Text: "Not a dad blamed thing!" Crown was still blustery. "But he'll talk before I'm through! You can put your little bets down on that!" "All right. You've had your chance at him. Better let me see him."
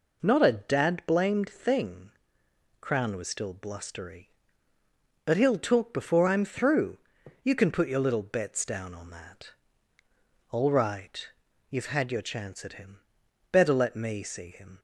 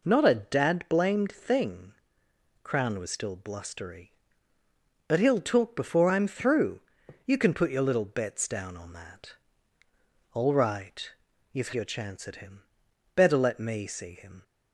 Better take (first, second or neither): first